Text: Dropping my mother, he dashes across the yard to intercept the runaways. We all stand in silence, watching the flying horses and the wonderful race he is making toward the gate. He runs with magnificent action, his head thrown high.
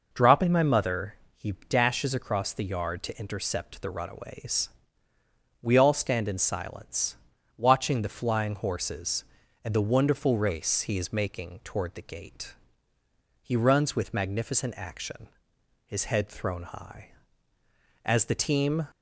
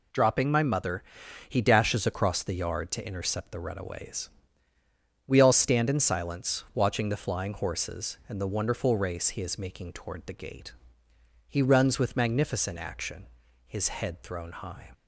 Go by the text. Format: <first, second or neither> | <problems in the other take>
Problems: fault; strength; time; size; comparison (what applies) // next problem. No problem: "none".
second | pauses between "he" and "dashes"; slight; at 1.5 s; 0.16 s long // goes on to say "As the team"; noticeable; from 18.0 s on; 0.82 s long